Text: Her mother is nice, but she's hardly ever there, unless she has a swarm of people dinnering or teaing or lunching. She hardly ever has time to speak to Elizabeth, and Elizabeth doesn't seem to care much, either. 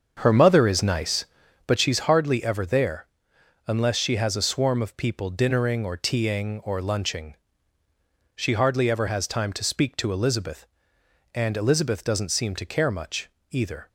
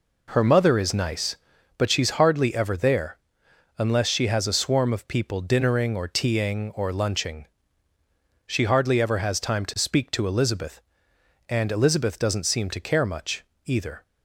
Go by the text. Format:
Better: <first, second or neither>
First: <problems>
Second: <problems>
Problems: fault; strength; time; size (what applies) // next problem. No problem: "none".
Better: second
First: starts louder than the rest; until 1.9 s; 7 dB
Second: none